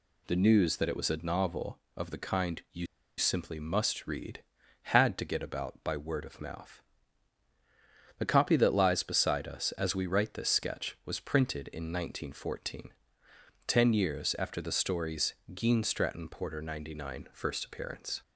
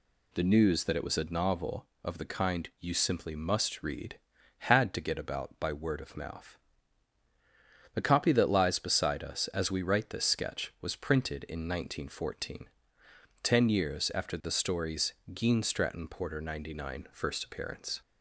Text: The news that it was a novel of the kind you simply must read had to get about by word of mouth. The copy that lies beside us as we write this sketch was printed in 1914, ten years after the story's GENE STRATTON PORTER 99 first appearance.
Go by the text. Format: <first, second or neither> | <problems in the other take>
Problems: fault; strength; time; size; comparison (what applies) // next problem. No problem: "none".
second | pauses between "you" and "simply"; slight; at 2.8 s; 0.31 s long // pauses between "story's" and "GENE"; slight; at 15.3 s; 0.20 s long; slight in the second